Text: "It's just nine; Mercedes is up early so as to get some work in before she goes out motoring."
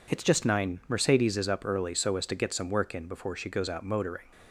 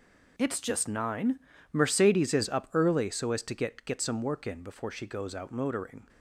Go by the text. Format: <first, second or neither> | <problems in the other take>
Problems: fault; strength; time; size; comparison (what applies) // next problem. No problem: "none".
first | says "get" twice; at 3.8 s